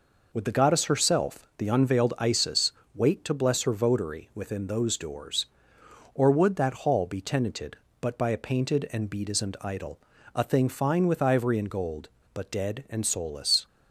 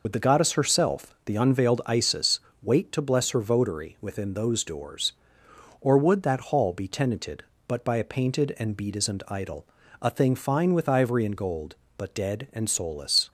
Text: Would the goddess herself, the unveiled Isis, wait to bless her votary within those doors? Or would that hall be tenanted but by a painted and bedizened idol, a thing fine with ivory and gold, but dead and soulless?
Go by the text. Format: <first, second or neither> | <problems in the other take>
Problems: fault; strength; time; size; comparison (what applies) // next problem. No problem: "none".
first | loses the start of "Would"; at 0.0 s; 35 ms